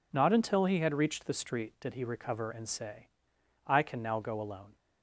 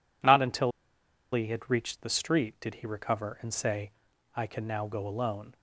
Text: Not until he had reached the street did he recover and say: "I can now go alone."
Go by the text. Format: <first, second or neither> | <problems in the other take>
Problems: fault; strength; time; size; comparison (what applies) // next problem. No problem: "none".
first | pauses between "until" and "he"; noticeable; at 0.7 s; 0.62 s long